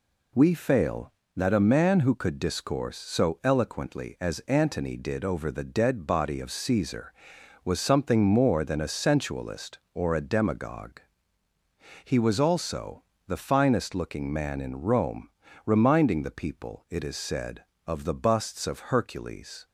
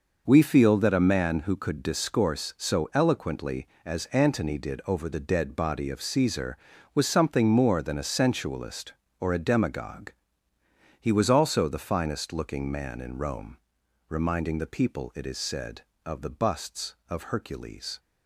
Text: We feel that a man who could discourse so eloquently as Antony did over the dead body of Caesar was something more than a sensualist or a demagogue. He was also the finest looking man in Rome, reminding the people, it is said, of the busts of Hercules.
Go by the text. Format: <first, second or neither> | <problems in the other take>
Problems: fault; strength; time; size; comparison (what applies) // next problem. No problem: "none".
second | says "fail" for "feel"; at 0.5 s // pauses between "also" and "the"; slight; at 13.0 s; 0.24 s long